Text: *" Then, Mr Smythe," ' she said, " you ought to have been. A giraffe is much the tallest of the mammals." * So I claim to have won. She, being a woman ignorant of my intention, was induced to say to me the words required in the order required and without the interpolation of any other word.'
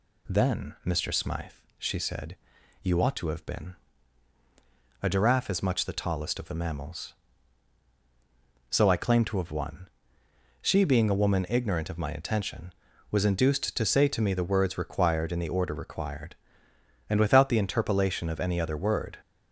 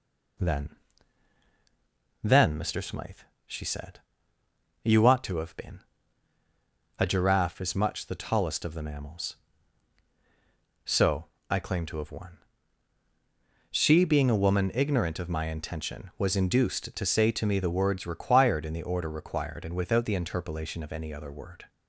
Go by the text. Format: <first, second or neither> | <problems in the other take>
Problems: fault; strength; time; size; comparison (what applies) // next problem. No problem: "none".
first | says "Then" twice; at 2.2 s // pauses between "So" and "I"; slight; at 11.2 s; 0.22 s long